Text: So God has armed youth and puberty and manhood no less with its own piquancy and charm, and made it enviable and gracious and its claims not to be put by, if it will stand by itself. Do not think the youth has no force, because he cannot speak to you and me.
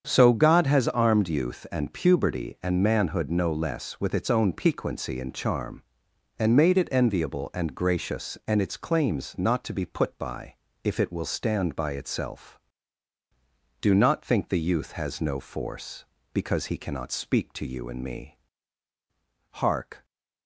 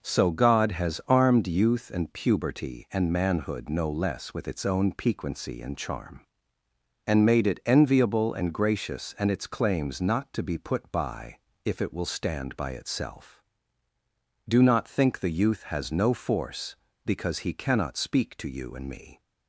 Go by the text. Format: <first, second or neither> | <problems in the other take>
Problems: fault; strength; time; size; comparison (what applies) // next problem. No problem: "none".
second | starts louder than the rest; strong; until 1.0 s; 7.5 dB // goes on to say "Hark"; from 19.5 s on; 0.52 s long